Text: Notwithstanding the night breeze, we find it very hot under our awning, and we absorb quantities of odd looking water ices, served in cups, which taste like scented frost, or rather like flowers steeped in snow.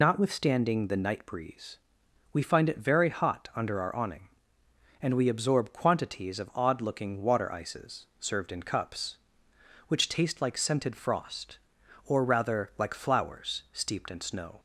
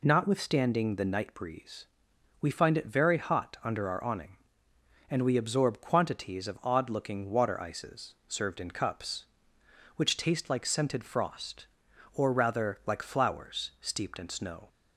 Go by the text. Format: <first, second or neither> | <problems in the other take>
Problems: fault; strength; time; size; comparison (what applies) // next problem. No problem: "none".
second | loses the start of "Notwithstanding"; at 0.0 s; 65 ms